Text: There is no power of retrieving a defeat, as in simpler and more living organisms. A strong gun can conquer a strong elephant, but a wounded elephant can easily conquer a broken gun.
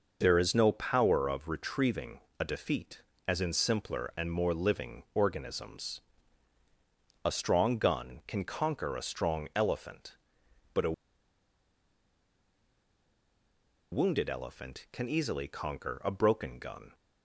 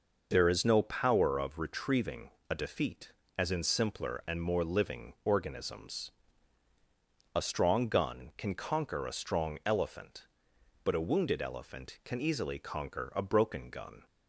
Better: second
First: pauses between "retrieving" and "a"; slight; at 2.1 s; 0.20 s long // pauses between "a" and "wounded"; strong; at 10.9 s; 3.0 s long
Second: pauses between "retrieving" and "a"; slight; at 2.2 s; 0.20 s long

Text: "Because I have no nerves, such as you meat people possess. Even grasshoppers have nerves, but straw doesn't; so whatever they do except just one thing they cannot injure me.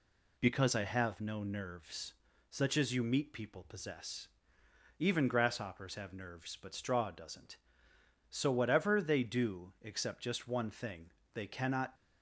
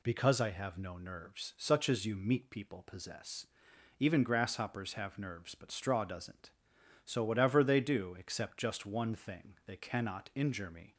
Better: second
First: pauses between "thing" and "they"; slight; at 11.1 s; 0.22 s long // stops before "injure me"; at 11.9 s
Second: none

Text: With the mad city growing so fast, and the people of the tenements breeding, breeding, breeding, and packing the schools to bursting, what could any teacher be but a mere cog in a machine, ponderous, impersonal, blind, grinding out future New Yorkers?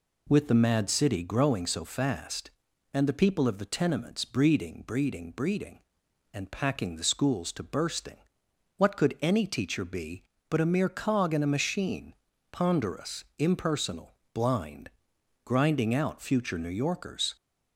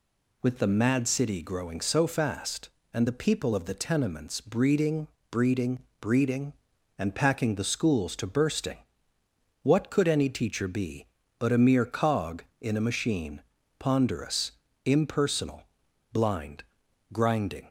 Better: first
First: none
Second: stops before "out future New Yorkers"; at 17.6 s

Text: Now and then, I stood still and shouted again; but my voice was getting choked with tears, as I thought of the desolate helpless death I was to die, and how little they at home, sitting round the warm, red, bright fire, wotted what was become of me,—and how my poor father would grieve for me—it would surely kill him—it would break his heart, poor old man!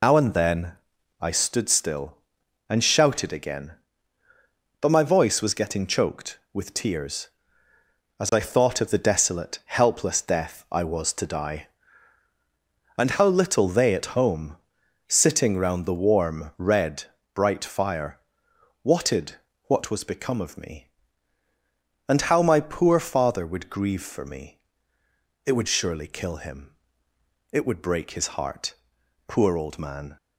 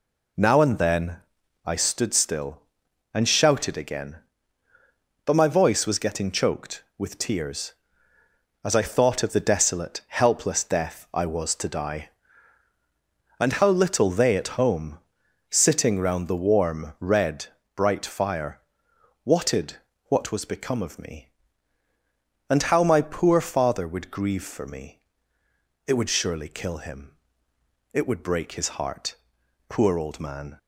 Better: second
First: loses the start of "Now"; at 0.0 s; 105 ms // pauses between "wotted" and "what"; slight; at 19.3 s; 0.34 s long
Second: pauses between "wotted" and "what"; slight; at 19.7 s; 0.34 s long

